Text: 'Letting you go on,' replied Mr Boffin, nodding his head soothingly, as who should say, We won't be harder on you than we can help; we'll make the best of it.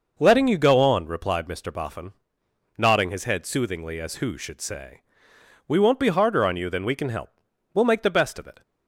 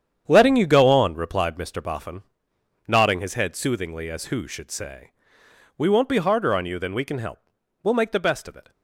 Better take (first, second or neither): first